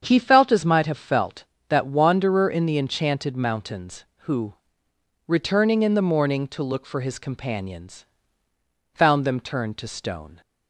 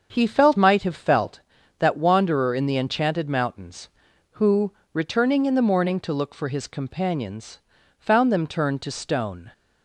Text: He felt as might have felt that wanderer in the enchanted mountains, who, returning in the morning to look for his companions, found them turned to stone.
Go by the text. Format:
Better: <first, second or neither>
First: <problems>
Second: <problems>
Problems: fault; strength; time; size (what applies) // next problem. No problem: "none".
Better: first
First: starts louder than the rest; strong; until 1.0 s; 7.5 dB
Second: starts louder than the rest; until 1.1 s; 6.5 dB // skips "as"; at 0.5 s